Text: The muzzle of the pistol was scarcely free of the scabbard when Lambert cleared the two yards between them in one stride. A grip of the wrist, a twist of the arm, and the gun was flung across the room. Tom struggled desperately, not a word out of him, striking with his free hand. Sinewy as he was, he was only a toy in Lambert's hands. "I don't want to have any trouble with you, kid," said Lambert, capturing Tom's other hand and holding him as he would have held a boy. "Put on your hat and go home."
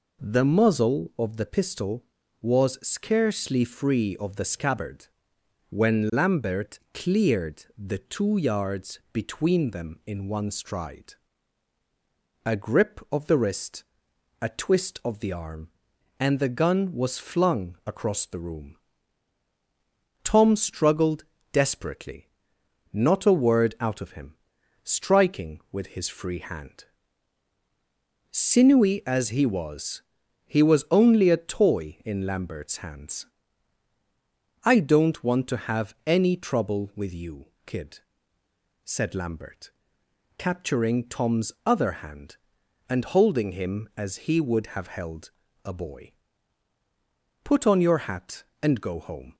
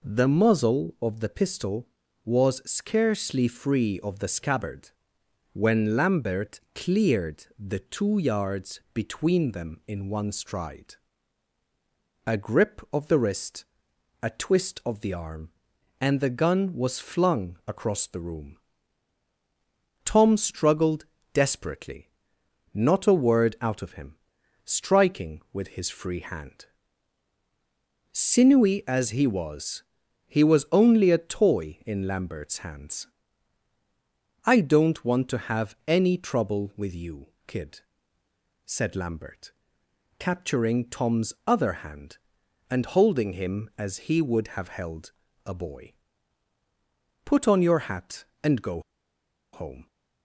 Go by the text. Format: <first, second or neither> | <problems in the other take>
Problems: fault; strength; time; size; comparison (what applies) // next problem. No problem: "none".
first | pauses between "scabbard" and "when"; noticeable; at 4.8 s; 0.62 s long; noticeable in the first // pauses between "Lambert" and "cleared"; slight; at 6.5 s; 0.16 s long; slight in the first // pauses between "struggled" and "desperately"; slight; at 21.0 s; 0.28 s long; slight in the first // pauses between "held" and "a"; slight; at 45.1 s; 0.32 s long; slight in the first // pauses between "go" and "home"; noticeable; at 48.7 s; 0.73 s long